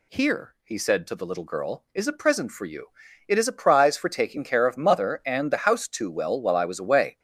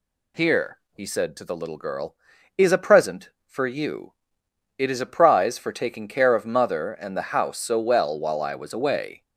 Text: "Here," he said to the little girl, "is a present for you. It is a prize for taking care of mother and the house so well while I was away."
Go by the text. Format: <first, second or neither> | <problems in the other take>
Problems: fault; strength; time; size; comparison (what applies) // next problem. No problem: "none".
second | says "too" for "so"; at 5.8 s